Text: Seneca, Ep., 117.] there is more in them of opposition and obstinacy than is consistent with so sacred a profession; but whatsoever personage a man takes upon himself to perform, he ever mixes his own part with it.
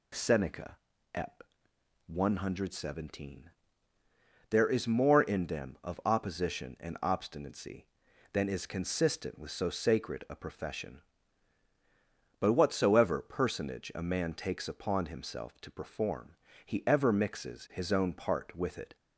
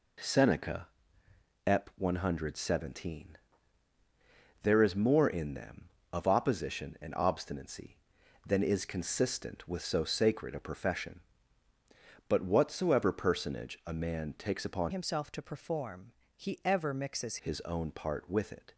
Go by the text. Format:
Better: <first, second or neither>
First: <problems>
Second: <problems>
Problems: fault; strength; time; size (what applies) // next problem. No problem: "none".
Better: first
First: none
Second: changes voice from "himself" to "mixes"; from 14.8 to 17.3 s; 2.5 s long